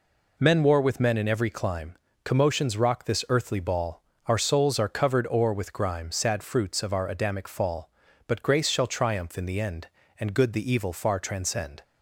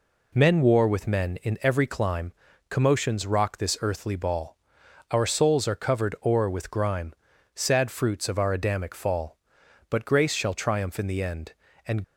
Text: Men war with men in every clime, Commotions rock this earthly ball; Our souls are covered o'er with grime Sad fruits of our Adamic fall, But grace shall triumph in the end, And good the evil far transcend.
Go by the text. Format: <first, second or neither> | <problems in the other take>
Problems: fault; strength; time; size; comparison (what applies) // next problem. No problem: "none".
first | pauses between "grime" and "Sad"; at 7.1 s; 0.40 s long // stops before "good the evil far transcend"; at 12.0 s